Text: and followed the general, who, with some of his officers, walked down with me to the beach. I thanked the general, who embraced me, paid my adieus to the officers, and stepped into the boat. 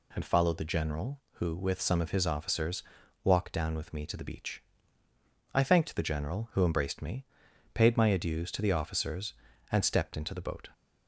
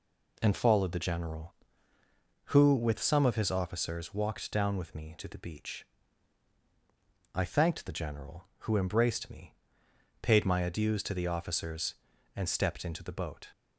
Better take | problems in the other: neither | none

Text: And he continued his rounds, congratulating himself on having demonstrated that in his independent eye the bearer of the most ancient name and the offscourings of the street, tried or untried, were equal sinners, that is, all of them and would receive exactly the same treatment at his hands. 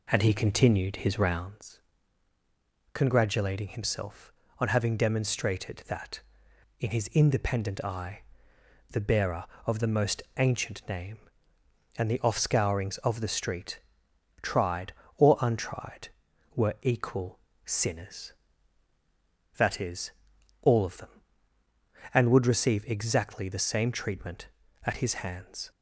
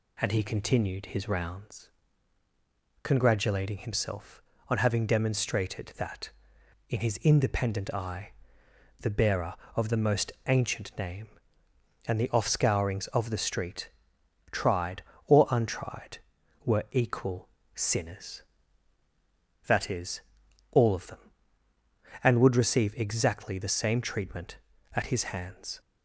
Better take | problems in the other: second | starts louder than the rest; slight; until 1.5 s; 3 dB // pauses between "eye" and "the"; noticeable; at 8.2 s; 0.68 s long; noticeable in the second // pauses between "most" and "ancient"; slight; at 10.2 s; 0.16 s long; slight in the second // pauses between "equal" and "sinners"; slight; at 17.3 s; 0.28 s long; slight in the second

